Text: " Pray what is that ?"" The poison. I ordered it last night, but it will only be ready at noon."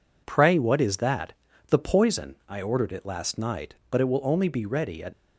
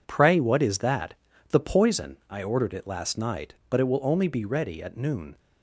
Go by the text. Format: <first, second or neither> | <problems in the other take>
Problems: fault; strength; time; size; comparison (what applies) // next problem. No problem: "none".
second | stops before "noon"; at 5.1 s